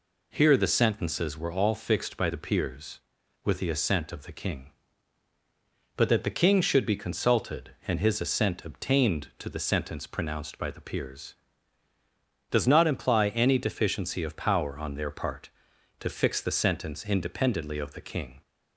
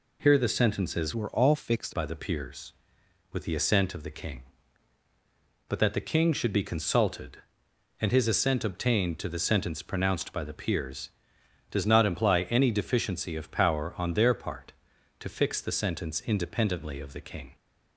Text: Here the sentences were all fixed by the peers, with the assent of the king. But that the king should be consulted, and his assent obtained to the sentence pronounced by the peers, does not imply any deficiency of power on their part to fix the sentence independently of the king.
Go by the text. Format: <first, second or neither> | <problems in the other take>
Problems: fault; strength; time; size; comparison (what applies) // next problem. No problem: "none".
first | changes voice from "were" to "fixed"; from 1.1 to 1.9 s; 0.8 s long